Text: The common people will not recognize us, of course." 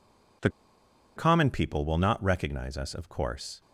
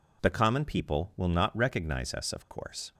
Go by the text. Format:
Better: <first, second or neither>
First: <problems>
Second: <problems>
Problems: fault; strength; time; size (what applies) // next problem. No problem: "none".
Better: second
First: pauses between "The" and "common"; noticeable; at 0.4 s; 0.67 s long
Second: none